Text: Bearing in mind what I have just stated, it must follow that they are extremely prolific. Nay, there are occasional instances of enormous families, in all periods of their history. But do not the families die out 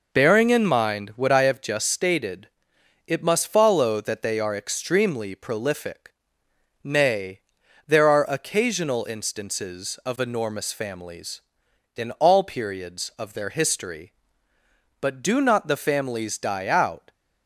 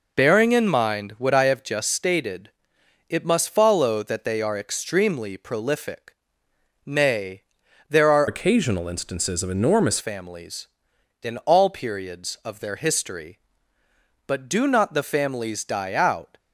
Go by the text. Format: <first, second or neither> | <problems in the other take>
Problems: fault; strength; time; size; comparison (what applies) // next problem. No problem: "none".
first | changes voice from "occasional" to "enormous"; from 8.2 to 9.9 s; 1.7 s long